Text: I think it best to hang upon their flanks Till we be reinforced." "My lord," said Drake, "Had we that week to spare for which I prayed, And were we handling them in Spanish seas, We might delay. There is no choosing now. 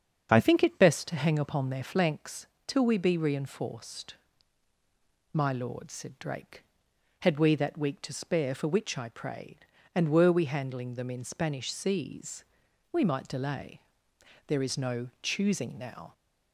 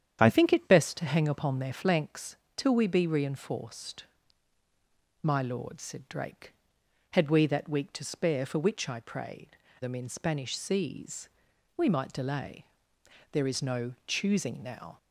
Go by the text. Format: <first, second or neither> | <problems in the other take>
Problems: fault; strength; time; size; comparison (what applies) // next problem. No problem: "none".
first | starts louder than the rest; strong; until 1.2 s; 9 dB; also in the first // pauses between "flanks" and "Till"; slight; at 2.3 s; 0.22 s long; slight in the first // skips "And were we handling"; at 9.6 s